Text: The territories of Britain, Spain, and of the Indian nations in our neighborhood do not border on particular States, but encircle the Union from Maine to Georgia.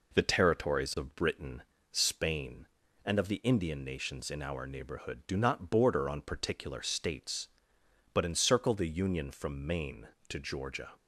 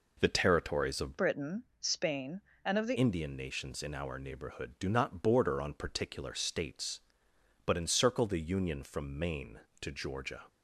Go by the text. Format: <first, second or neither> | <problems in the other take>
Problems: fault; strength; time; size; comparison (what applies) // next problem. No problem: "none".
first | changes voice from "Britain" to "the"; from 1.1 to 2.9 s; 1.8 s long